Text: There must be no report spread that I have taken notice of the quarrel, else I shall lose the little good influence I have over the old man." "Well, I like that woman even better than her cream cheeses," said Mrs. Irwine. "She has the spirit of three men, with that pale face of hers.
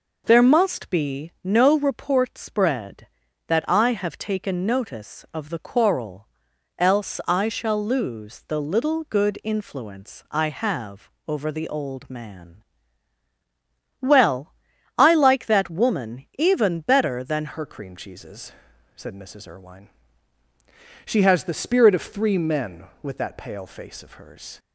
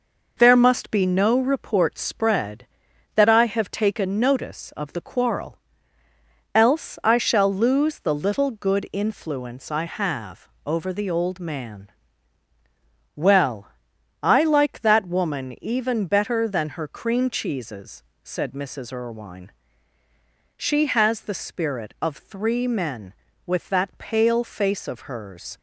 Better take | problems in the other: second | pauses between "have" and "over"; slight; at 11.0 s; 0.18 s long; slight in the second // changes voice at "her"; from 17.5 s on; 7.0 s long

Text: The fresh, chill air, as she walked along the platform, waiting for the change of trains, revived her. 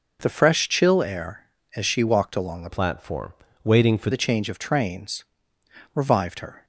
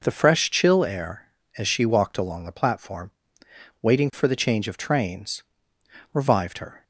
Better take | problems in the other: second | changes voice from "platform" to "for"; from 2.6 to 4.1 s; 1.5 s long

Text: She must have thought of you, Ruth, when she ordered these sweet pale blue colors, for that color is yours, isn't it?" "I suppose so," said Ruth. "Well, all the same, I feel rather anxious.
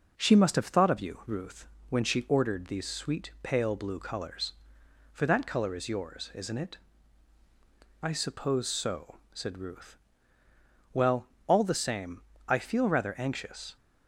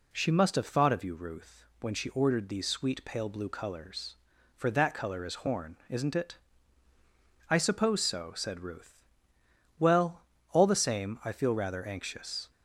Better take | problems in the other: first | says "horn" for "yours"; at 5.3 s

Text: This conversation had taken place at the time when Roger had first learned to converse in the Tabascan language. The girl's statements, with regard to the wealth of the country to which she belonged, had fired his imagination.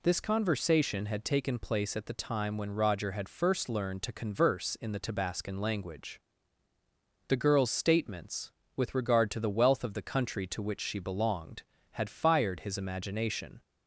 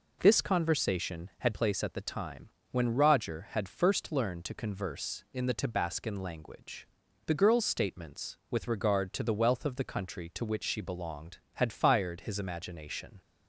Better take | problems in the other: first | skips "taken"; at 1.5 s // pauses between "time" and "when"; slight; at 2.4 s; 0.22 s long

